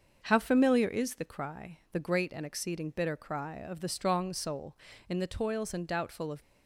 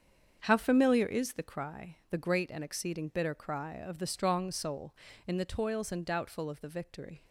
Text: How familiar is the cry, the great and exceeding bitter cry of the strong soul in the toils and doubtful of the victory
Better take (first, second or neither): second